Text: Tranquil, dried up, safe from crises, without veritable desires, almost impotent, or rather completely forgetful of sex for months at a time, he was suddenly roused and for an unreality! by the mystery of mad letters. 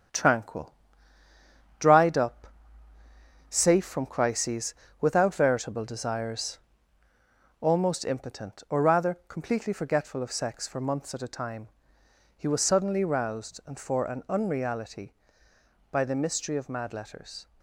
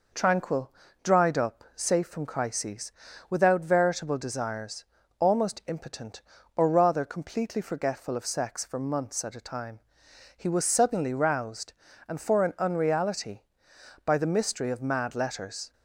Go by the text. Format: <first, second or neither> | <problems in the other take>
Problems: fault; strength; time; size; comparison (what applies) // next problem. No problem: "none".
second | gets quieter; noticeable; throughout; 4 dB